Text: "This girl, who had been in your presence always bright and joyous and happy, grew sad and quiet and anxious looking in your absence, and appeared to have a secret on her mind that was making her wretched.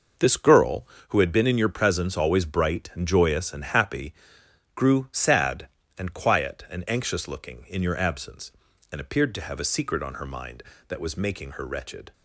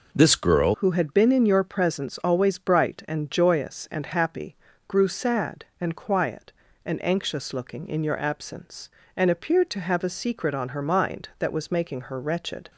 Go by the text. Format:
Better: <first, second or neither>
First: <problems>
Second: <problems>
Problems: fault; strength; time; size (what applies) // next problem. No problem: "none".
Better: first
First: none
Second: changes voice at "who"; from 0.7 s on; 12.0 s long